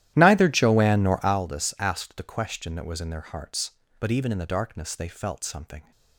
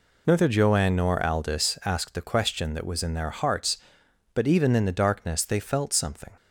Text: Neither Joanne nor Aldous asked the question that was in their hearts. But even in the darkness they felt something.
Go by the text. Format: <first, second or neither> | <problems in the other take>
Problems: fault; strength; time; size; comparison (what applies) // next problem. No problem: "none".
second | starts louder than the rest; strong; until 1.4 s; 13 dB